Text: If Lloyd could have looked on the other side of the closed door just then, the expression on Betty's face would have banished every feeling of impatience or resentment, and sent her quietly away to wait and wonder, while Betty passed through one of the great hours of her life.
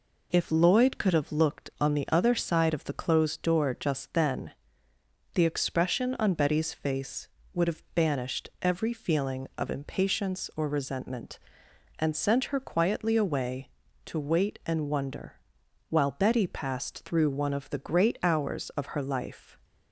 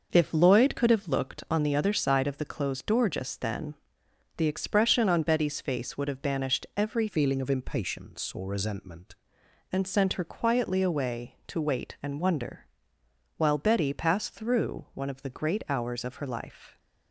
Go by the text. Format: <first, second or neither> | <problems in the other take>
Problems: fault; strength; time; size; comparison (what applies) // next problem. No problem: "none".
first | changes voice from "feeling" to "resentment"; from 7.0 to 9.1 s; 2.1 s long